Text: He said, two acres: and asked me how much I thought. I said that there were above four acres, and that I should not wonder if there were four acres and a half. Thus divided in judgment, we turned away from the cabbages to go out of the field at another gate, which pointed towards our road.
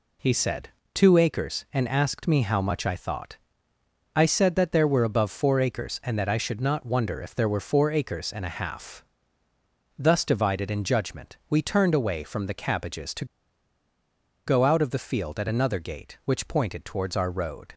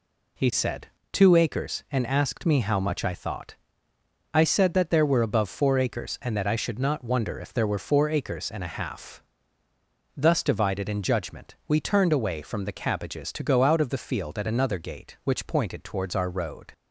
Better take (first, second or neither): second